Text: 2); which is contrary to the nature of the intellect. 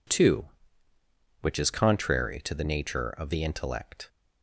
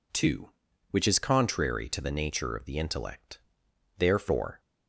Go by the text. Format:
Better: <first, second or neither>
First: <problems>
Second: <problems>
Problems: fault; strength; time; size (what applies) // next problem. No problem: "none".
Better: first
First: none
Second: goes on to say "Therefore"; noticeable; from 3.9 s on; 0.62 s long